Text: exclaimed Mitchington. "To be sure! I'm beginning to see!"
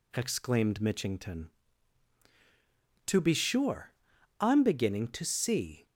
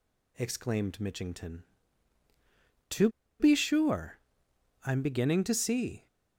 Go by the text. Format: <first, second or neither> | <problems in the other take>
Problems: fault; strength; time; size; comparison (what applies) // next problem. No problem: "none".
first | pauses between "To" and "be"; slight; at 3.0 s; 0.31 s long